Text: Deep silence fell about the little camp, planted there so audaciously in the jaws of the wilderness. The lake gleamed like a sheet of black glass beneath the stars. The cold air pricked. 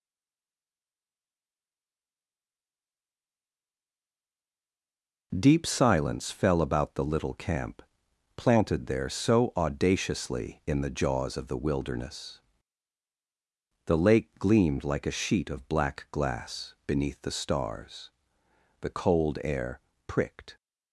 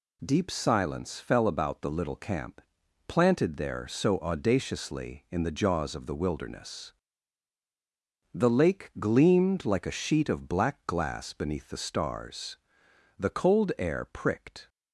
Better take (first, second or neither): second